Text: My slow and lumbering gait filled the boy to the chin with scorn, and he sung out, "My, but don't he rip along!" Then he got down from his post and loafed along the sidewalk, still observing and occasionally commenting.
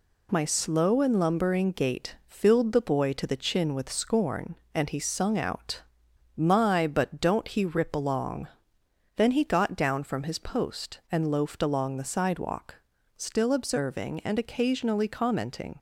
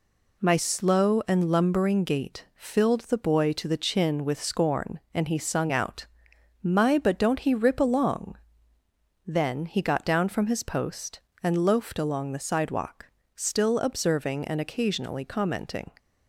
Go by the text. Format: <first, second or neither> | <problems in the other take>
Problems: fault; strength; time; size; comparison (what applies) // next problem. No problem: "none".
neither | none